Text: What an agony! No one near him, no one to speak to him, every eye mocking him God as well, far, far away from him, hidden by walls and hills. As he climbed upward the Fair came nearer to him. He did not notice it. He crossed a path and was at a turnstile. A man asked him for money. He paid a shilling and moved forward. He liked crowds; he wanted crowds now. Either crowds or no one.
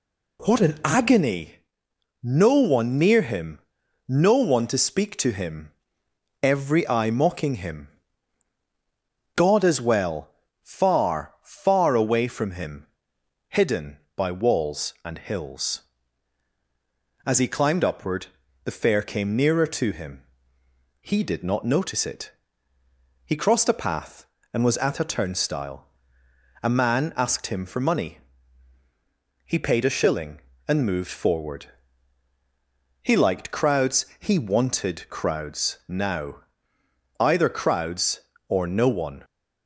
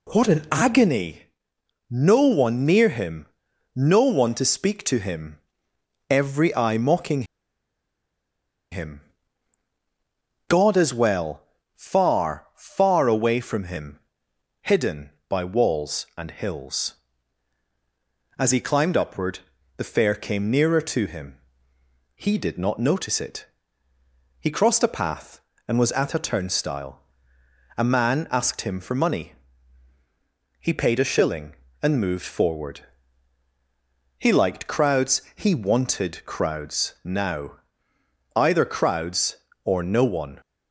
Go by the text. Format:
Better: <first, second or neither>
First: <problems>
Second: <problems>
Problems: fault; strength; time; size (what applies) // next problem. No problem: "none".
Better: first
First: pauses between "him" and "God"; strong; at 7.8 s; 1.4 s long // pauses between "upward" and "the"; at 18.2 s; 0.40 s long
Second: pauses between "mocking" and "him"; strong; at 7.2 s; 1.4 s long // pauses between "him" and "God"; strong; at 9.0 s; 1.4 s long // pauses between "upward" and "the"; at 19.3 s; 0.40 s long